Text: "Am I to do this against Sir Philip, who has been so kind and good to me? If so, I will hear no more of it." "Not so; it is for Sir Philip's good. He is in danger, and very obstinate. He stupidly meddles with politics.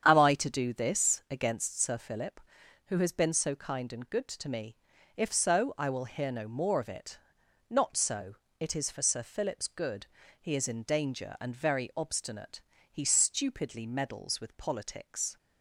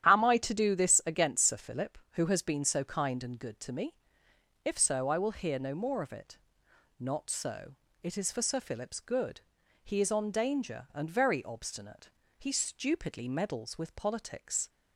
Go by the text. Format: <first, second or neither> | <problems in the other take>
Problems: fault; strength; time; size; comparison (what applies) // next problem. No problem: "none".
first | starts louder than the rest; strong; until 1.1 s; 10 dB; strong in the first // says "on" for "in"; at 10.1 s